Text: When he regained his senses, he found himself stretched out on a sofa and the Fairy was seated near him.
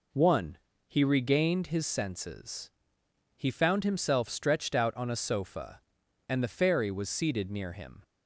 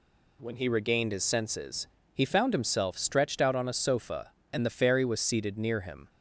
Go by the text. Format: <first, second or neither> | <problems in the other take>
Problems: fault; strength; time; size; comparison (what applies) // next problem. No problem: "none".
second | says "One" for "When"; at 0.1 s